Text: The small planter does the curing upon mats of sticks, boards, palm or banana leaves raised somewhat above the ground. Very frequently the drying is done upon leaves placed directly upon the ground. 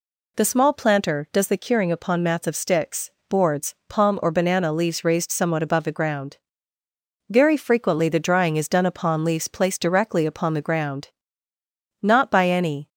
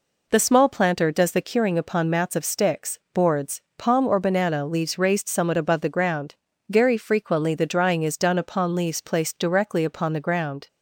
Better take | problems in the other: second | goes on to say "Not by any"; noticeable; from 12.0 s on; 0.86 s long

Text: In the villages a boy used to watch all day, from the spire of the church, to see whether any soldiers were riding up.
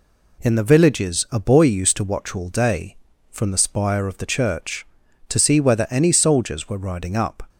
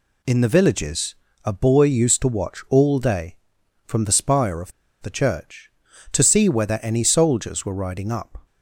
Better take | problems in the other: first | pauses between "villages" and "a"; slight; at 1.1 s; 0.26 s long // pauses between "of" and "the"; slight; at 4.7 s; 0.29 s long

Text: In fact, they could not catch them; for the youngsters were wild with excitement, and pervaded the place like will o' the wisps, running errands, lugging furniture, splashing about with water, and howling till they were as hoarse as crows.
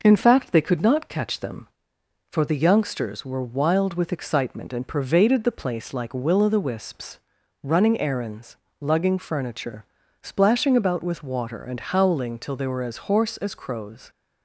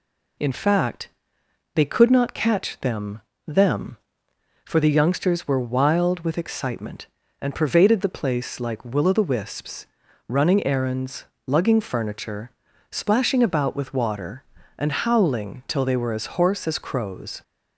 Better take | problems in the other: first | says "them" twice; at 3.4 s

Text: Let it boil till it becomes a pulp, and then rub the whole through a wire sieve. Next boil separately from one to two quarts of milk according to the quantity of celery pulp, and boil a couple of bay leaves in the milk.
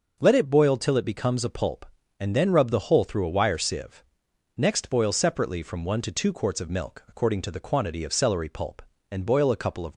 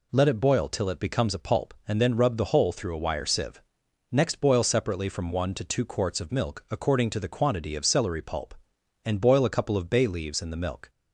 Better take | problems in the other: second | stops before "bay leaves in the milk"; at 9.9 s

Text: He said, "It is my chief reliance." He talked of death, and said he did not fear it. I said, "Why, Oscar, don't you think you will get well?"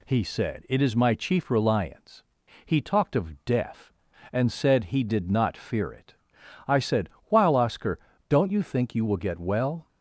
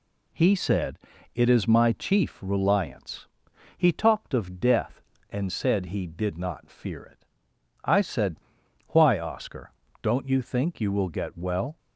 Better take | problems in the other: second | says "While" for "Why"; at 7.2 s

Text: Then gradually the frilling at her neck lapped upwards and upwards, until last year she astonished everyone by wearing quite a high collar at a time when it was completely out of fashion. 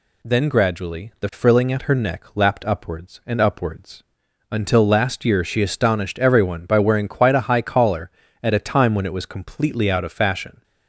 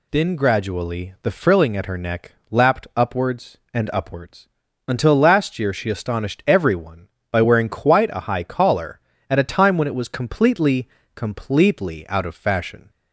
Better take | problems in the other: first | pauses between "neck" and "lapped"; slight; at 2.3 s; 0.18 s long // says "completely" twice; at 11.1 s

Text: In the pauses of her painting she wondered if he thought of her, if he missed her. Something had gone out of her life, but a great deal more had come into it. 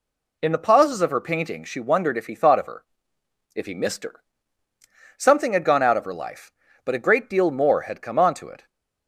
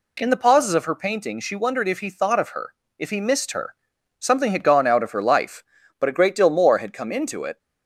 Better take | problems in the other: second | says "onto" for "into"; at 8.1 s

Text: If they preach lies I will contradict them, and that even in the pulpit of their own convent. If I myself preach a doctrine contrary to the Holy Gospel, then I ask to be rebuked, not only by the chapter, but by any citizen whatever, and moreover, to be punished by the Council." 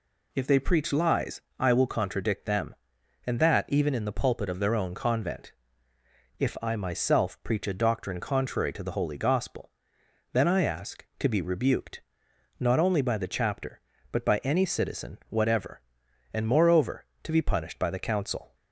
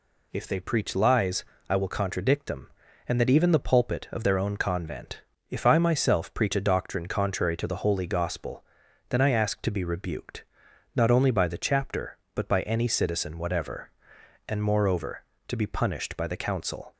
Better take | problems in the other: first | pauses between "lies" and "I"; slight; at 1.4 s; 0.24 s long; slight in the first // skips "in"; at 3.5 s

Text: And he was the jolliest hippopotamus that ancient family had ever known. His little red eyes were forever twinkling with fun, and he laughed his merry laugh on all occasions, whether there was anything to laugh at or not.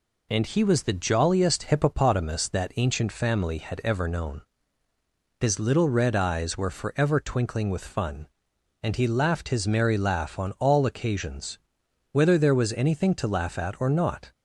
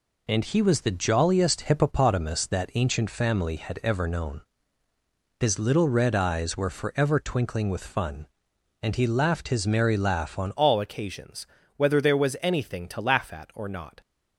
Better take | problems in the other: first | changes voice at "all"; from 10.5 s on; 3.5 s long

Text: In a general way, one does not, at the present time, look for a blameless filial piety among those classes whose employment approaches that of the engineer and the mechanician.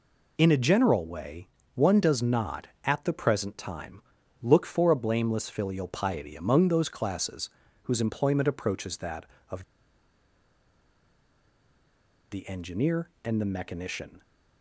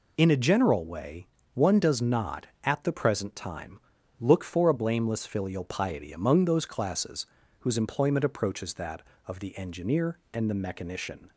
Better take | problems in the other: second | pauses between "classes" and "whose"; slight; at 7.4 s; 0.36 s long; slight in the second // pauses between "of" and "the"; strong; at 9.6 s; 2.6 s long

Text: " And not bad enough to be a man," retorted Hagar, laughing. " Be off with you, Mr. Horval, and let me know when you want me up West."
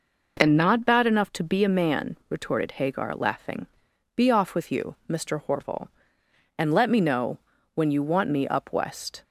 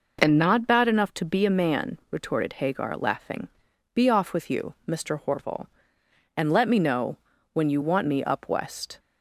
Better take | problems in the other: neither | pauses between "know" and "when"; the same in both

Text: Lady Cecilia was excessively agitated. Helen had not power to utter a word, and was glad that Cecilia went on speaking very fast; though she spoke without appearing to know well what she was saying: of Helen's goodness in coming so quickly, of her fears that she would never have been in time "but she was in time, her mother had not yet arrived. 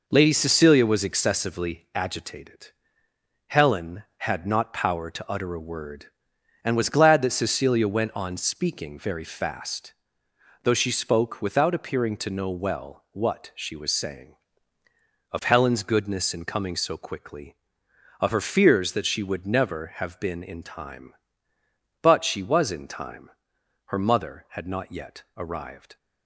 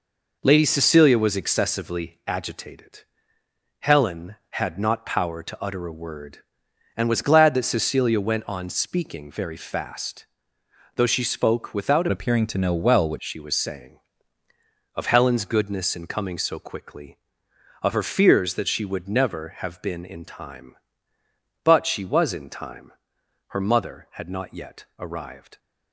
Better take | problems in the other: first | changes voice from "appearing" to "what"; from 12.1 to 13.1 s; 1.0 s long

